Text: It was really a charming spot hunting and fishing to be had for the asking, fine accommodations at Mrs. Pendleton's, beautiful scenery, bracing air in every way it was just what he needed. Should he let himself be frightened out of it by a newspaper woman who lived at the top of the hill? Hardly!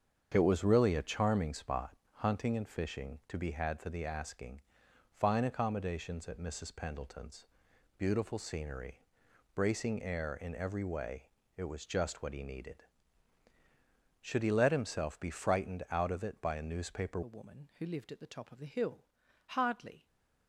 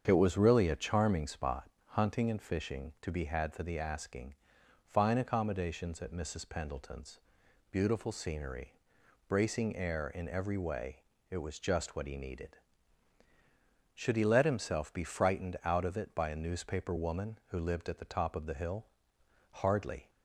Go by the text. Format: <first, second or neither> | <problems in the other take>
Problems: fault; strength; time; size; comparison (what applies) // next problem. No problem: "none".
second | starts louder than the rest; strong; until 1.3 s; 7.5 dB; strong in the second // pauses between "spot" and "hunting"; slight; at 1.9 s; 0.22 s long; slight in the second // pauses between "way" and "it"; slight; at 11.2 s; 0.30 s long; slight in the second // changes voice at "woman"; from 17.2 s on; 2.8 s long // stays silent after the last word; slight; from 19.9 s on; 0.5 s long